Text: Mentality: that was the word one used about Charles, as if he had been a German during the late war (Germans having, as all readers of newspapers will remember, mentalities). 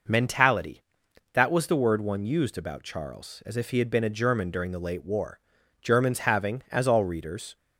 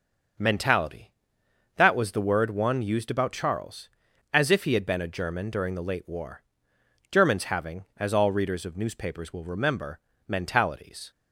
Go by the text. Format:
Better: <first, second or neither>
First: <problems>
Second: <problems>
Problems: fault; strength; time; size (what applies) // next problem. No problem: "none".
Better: second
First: stops before "of newspapers will remember mentalities"; at 7.5 s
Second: none